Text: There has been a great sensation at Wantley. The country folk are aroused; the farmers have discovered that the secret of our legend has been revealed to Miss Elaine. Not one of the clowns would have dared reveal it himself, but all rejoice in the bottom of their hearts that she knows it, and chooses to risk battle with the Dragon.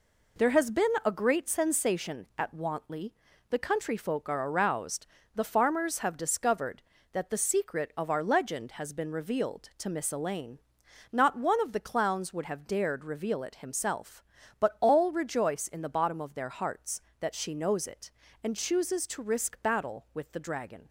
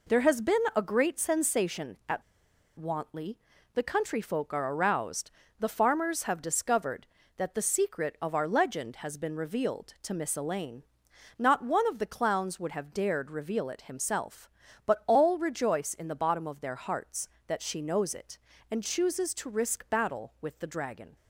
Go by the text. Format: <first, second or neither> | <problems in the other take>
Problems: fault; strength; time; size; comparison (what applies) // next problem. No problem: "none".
first | pauses between "been" and "a"; slight; at 0.5 s; 0.18 s long; slight in the first // pauses between "at" and "Wantley"; noticeable; at 2.2 s; 0.56 s long